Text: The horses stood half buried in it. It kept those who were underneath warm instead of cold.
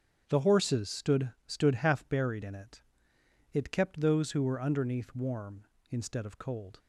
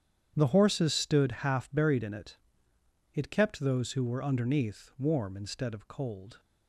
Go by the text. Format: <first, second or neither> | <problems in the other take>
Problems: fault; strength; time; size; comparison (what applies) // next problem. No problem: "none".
second | starts louder than the rest; strong; until 1.2 s; 8.5 dB; strong in the second // says "stood" twice; at 1.4 s